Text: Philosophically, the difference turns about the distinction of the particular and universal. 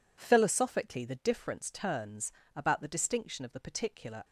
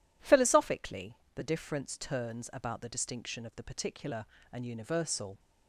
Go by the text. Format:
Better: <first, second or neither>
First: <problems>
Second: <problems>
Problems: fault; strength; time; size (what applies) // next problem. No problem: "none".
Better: second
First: pauses between "turns" and "about"; slight; at 2.3 s; 0.20 s long // stops before "and universal"; at 4.2 s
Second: none